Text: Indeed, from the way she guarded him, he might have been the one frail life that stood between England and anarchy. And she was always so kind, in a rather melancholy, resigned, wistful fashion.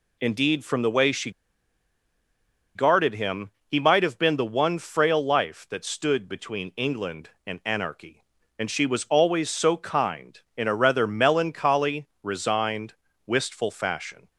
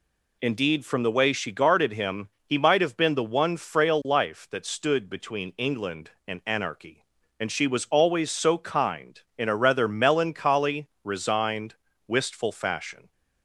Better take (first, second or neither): second